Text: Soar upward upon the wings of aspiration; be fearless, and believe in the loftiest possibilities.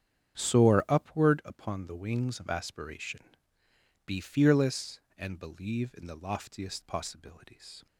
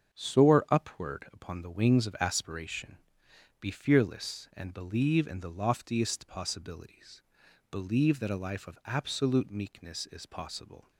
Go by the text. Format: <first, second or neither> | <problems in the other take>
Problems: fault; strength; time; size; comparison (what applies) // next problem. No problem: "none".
first | starts louder than the rest; strong; until 1.1 s; 7 dB; strong in the first // goes on to say "Believe that a life of absolute meekness is possible"; strong; from 7.6 s on; 3.2 s long